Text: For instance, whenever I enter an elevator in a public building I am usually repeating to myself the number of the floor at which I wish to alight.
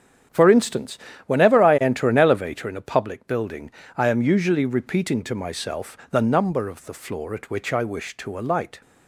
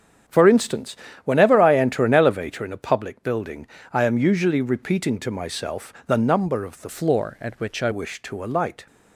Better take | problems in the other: first | starts louder than the rest; strong; until 1.5 s; 8 dB; strong in the first // pauses between "building" and "I"; slight; at 3.6 s; 0.28 s long; slight in the first // changes voice from "floor" to "I"; from 6.8 to 7.8 s; 1.0 s long

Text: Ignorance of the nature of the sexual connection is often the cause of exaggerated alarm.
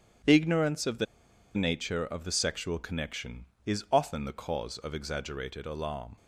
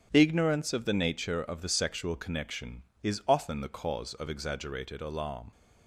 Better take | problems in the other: second | starts louder than the rest; strong; until 1.7 s; 9.5 dB; strong in the second // pauses between "the" and "nature"; noticeable; at 1.0 s; 0.50 s long

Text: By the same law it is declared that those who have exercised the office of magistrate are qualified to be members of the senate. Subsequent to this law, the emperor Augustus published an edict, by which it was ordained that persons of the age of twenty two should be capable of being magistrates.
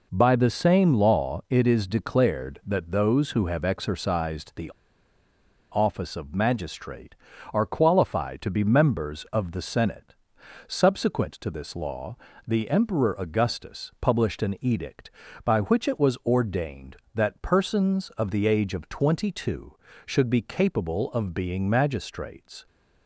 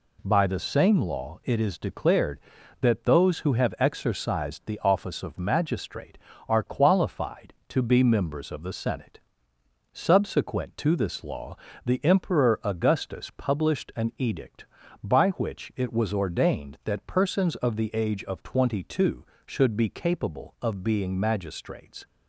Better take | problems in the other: second | pauses between "the" and "office"; at 4.7 s; 1.0 s long

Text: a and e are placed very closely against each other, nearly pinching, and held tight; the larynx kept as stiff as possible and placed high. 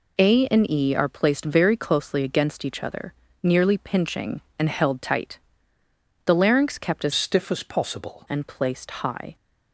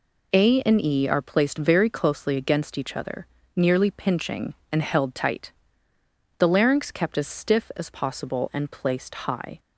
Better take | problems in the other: second | changes voice from "stiff" to "possible"; from 7.1 to 8.2 s; 1.1 s long

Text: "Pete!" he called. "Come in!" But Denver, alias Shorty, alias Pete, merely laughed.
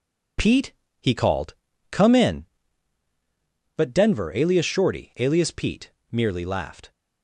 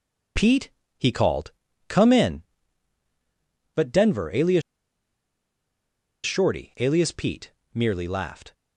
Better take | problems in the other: first | pauses between "alias" and "Shorty"; strong; at 4.6 s; 1.6 s long

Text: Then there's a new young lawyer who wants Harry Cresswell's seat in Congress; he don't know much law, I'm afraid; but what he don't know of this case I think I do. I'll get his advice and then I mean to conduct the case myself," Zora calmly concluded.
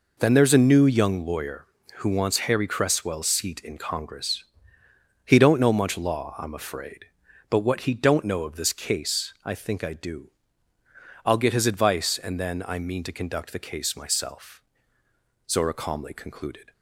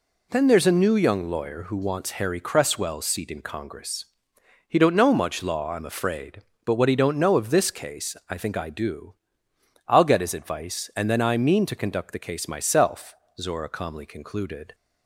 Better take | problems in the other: neither | none

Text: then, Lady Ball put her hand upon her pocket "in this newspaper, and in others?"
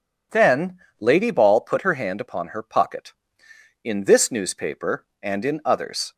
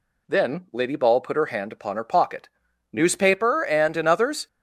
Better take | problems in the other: first | skips "in this"; at 2.6 s

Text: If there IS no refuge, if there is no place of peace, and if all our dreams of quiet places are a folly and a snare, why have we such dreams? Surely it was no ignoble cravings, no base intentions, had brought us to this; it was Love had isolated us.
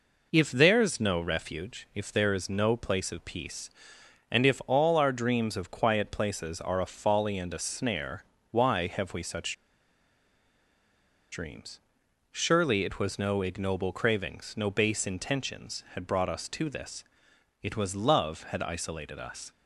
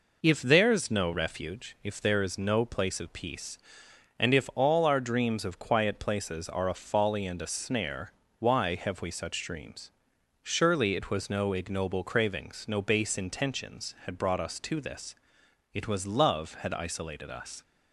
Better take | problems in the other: second | pauses between "such" and "dreams"; strong; at 9.5 s; 1.7 s long

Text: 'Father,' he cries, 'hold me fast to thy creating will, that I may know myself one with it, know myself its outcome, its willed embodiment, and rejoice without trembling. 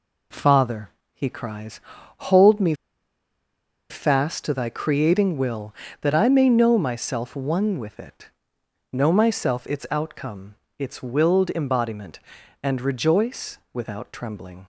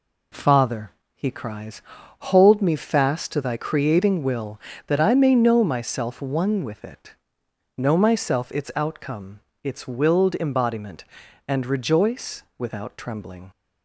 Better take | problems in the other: second | pauses between "me" and "fast"; at 2.7 s; 1.1 s long

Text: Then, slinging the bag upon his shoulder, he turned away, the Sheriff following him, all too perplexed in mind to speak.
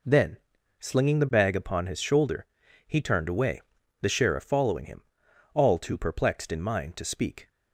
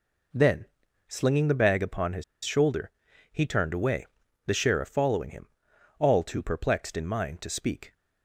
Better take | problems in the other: first | pauses between "his" and "shoulder"; slight; at 2.2 s; 0.21 s long

